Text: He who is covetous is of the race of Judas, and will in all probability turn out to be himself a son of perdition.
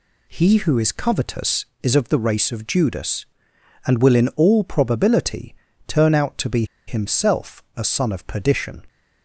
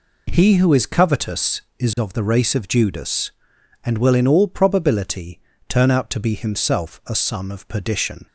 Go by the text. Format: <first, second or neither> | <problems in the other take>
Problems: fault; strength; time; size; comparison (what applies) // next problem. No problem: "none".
second | pauses between "probability" and "turn"; slight; at 5.5 s; 0.32 s long; slight in the second // pauses between "be" and "himself"; slight; at 6.6 s; 0.22 s long